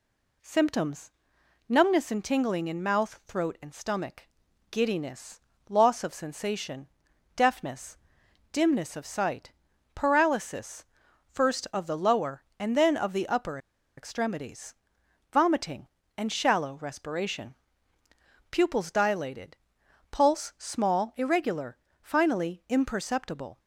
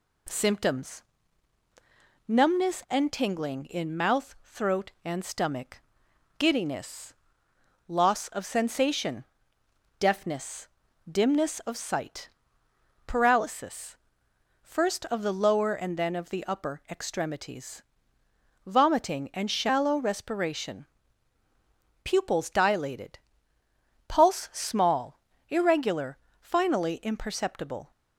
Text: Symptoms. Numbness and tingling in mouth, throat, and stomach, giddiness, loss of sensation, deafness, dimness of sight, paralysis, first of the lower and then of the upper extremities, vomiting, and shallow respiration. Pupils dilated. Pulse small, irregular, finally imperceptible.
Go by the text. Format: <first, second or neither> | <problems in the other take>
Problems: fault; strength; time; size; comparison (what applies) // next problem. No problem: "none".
second | pauses between "upper" and "extremities"; at 13.5 s; 0.39 s long